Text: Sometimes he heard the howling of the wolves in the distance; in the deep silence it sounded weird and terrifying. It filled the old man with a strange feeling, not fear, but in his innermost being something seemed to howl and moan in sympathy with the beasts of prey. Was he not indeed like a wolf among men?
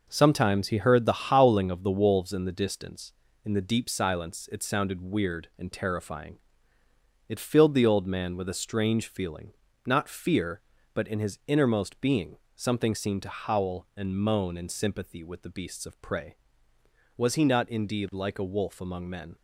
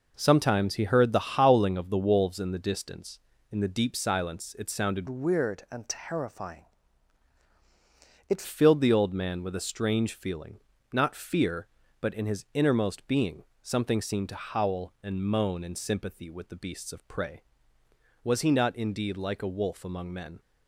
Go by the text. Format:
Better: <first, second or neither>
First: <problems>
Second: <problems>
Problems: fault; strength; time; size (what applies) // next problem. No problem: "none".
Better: first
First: pauses between "being" and "something"; slight; at 12.3 s; 0.18 s long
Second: changes voice from "weird" to "It"; from 5.0 to 8.4 s; 3.4 s long // pauses between "being" and "something"; slight; at 13.4 s; 0.18 s long